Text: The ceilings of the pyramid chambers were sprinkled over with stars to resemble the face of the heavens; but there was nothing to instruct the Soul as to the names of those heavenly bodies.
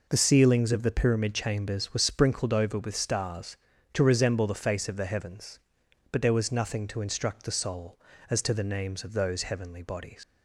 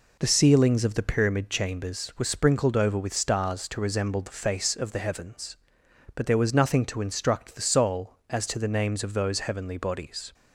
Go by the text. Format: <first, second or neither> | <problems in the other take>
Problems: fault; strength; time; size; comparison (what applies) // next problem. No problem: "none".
second | leaves "bodies" unfinished; at 10.2 s; 120 ms